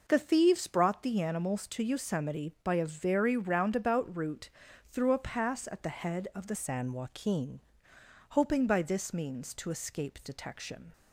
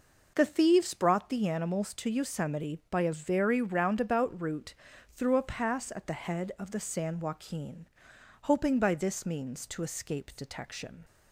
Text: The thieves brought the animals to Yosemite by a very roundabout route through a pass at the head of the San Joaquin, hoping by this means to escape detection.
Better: second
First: pauses between "route" and "through"; slight; at 4.5 s; 0.36 s long // changes voice from "San" to "Joaquin"; from 6.5 to 7.5 s; 1.0 s long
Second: pauses between "route" and "through"; slight; at 4.7 s; 0.35 s long

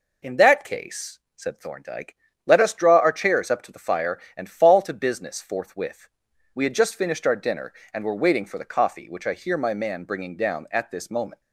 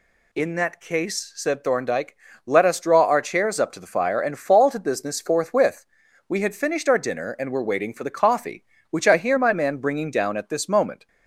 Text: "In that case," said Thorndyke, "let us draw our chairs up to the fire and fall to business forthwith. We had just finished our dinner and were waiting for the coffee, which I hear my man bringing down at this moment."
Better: first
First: none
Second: skips "just"; at 6.5 s

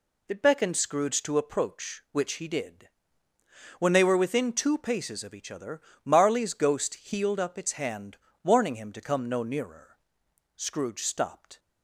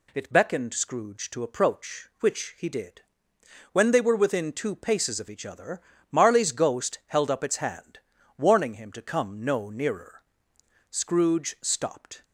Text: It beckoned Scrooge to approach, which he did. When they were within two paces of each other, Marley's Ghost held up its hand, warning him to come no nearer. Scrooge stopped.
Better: second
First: says "healed" for "held"; at 6.9 s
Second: none

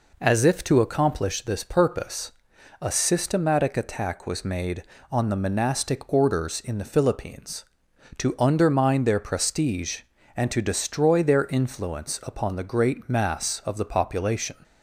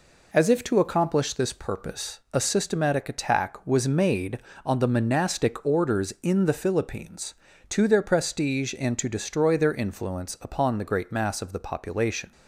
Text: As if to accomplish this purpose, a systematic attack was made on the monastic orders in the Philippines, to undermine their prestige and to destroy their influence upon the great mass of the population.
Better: first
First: none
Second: skips "undermine"; at 7.8 s

